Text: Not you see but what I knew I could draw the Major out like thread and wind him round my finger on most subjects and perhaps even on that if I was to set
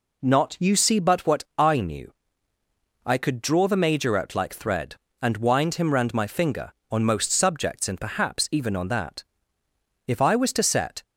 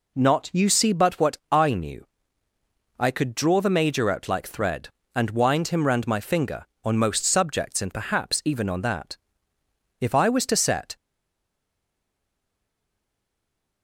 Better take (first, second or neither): first